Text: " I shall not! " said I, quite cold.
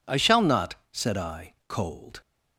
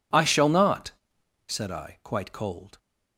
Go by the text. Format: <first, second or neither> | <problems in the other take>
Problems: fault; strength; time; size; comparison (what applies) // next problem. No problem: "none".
second | skips "quite"; at 1.6 s